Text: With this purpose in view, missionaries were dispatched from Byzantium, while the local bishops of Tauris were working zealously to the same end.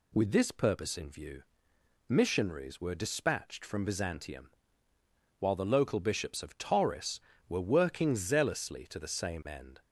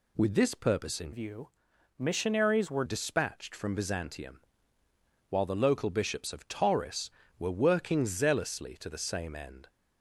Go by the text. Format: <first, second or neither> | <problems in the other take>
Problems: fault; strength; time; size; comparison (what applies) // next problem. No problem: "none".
first | changes voice from "view" to "were"; from 1.1 to 2.8 s; 1.7 s long